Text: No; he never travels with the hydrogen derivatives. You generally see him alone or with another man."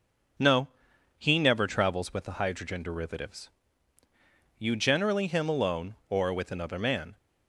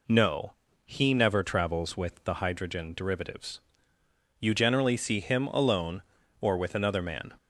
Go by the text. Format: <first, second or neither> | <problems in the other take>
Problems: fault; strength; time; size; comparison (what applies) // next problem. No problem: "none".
second | starts louder than the rest; until 1.8 s; 6.5 dB // skips "see"; at 5.2 s